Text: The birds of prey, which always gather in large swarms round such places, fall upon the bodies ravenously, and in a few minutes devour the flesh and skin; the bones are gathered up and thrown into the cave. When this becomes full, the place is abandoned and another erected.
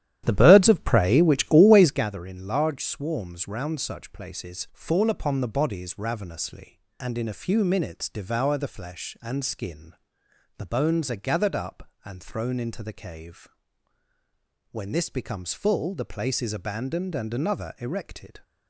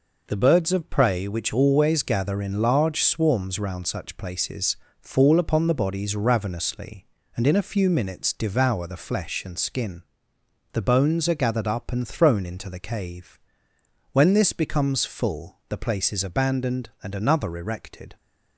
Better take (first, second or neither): second